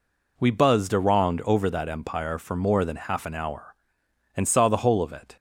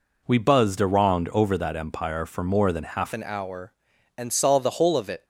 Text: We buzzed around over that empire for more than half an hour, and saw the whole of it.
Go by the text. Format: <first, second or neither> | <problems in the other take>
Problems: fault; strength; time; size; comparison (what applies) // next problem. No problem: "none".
first | changes voice at "an"; from 3.1 s on; 2.1 s long